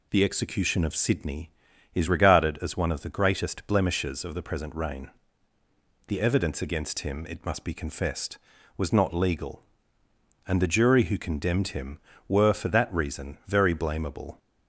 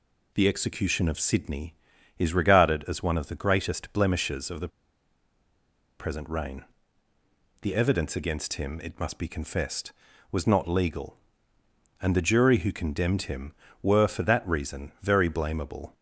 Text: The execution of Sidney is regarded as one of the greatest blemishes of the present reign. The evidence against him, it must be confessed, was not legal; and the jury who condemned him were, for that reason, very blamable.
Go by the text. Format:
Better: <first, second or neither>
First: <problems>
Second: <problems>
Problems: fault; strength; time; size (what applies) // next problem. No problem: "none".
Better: first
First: none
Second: pauses between "the" and "present"; strong; at 4.6 s; 1.3 s long